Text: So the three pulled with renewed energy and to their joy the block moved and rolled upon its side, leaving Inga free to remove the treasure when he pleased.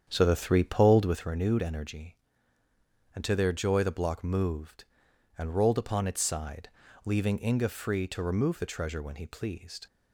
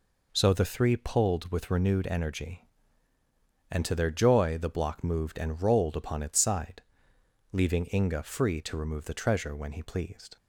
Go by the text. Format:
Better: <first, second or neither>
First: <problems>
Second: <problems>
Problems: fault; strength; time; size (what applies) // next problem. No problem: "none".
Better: second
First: starts louder than the rest; strong; until 1.3 s; 8.5 dB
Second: none